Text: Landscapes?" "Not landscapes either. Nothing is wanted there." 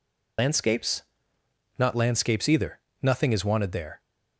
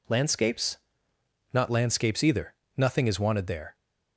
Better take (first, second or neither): second